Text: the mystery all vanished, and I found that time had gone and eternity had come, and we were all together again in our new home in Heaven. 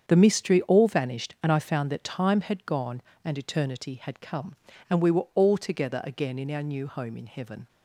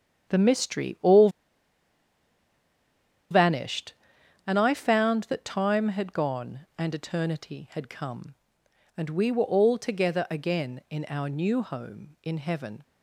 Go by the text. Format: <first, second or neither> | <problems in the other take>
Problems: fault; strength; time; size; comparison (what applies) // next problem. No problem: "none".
first | starts louder than the rest; strong; until 3.3 s; 8 dB; strong in the first // pauses between "all" and "vanished"; strong; at 1.2 s; 2.0 s long